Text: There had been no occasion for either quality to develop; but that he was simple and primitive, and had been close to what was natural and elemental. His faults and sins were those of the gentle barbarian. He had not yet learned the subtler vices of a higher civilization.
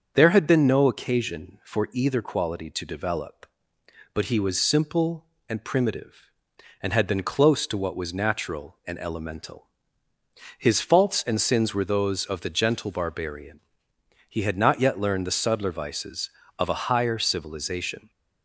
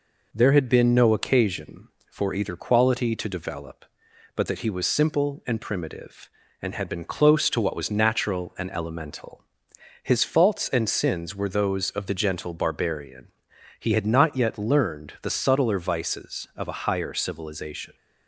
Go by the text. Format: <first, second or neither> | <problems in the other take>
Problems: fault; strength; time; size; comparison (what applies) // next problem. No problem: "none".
second | starts louder than the rest; until 1.1 s; 7 dB // skips "that"; at 4.2 s